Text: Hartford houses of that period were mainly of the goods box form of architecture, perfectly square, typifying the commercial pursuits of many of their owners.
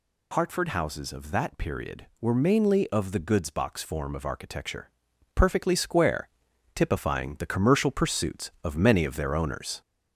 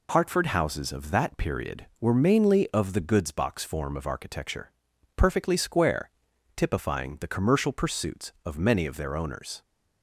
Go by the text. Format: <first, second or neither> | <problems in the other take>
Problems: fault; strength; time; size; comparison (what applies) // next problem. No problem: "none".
second | gets louder; throughout; 3.5 dB